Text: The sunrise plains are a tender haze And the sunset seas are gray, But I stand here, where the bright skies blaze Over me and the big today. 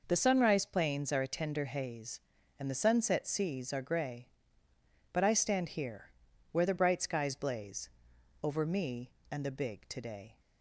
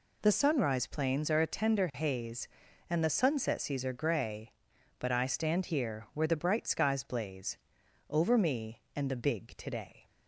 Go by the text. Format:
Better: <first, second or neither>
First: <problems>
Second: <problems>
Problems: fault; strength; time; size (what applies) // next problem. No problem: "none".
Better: neither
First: pauses between "blaze" and "Over"; noticeable; at 7.8 s; 0.54 s long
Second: pauses between "blaze" and "Over"; noticeable; at 7.5 s; 0.52 s long